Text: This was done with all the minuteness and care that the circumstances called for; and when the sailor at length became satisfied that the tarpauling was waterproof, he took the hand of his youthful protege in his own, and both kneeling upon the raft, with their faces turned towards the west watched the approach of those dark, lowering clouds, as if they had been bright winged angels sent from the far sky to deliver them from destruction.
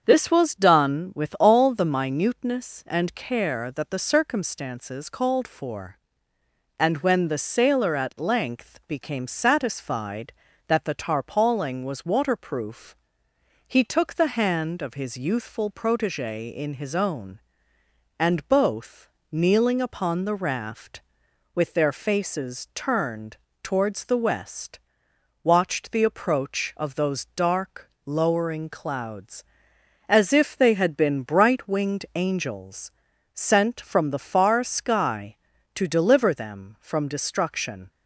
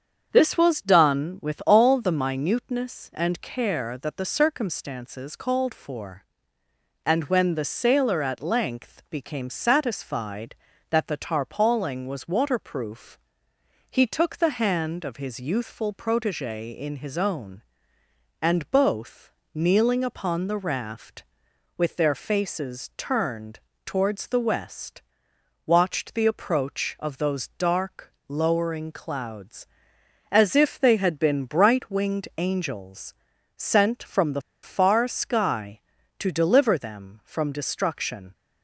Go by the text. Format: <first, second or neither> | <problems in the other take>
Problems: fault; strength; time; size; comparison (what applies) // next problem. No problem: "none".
first | starts louder than the rest; strong; until 1.3 s; 7.5 dB; strong in the first // pauses between "both" and "kneeling"; slight; at 19.3 s; 0.20 s long; slight in the first // pauses between "turned" and "towards"; slight; at 23.5 s; 0.26 s long; slight in the first // pauses between "west" and "watched"; noticeable; at 25.0 s; 0.64 s long; noticeable in the first // pauses between "angels" and "sent"; at 33.1 s; 0.42 s long; also in the first // pauses between "the" and "far"; slight; at 34.4 s; 0.22 s long